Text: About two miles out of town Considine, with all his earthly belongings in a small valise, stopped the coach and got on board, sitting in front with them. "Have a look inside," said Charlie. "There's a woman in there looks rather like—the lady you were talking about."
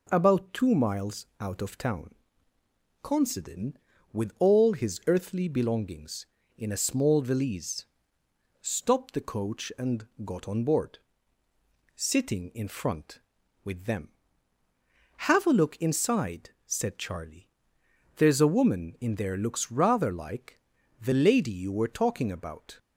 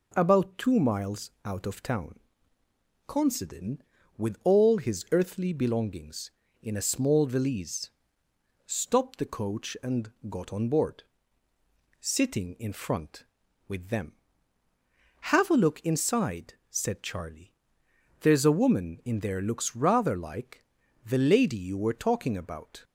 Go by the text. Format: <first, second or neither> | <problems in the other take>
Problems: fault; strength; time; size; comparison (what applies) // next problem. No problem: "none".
neither | pauses between "town" and "Considine"; noticeable; the same in both // pauses between "and" and "got"; slight; the same in both